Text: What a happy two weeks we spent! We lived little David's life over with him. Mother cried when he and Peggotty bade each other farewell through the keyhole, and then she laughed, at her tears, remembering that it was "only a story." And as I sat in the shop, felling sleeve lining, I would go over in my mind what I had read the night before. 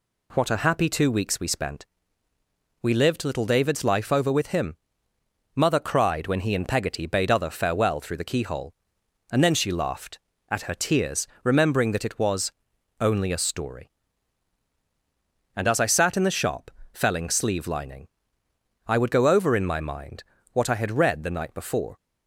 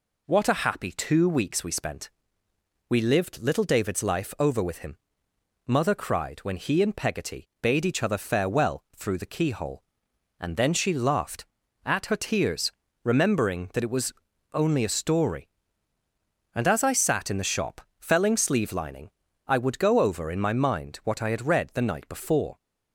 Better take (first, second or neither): second